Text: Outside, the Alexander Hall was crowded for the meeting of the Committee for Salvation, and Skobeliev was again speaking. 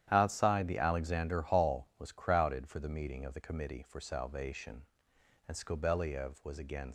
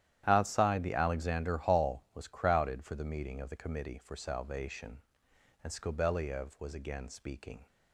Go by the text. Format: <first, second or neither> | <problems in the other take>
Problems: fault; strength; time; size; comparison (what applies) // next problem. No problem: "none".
second | starts louder than the rest; strong; until 1.1 s; 11 dB; strong in the second // stops before "speaking"; at 6.8 s